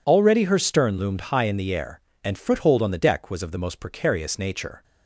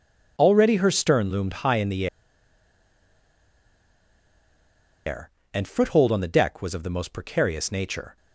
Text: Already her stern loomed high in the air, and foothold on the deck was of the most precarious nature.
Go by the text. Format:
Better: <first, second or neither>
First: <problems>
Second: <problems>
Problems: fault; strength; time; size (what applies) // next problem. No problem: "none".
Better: first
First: none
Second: pauses between "the" and "air"; strong; at 2.0 s; 2.9 s long